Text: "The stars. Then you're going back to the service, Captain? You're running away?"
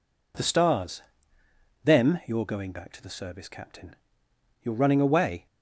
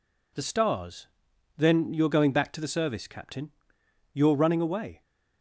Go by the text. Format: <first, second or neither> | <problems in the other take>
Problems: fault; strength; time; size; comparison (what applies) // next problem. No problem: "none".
second | says "Them" for "Then"; at 1.8 s